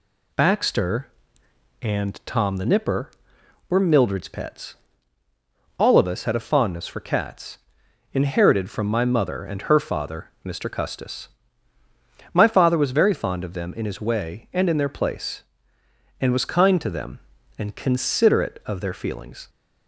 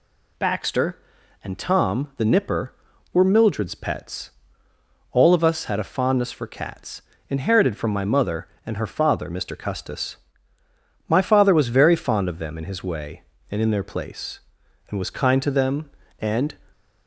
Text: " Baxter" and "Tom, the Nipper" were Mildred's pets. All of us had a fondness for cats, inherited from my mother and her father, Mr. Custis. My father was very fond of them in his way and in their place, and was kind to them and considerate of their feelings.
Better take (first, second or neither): first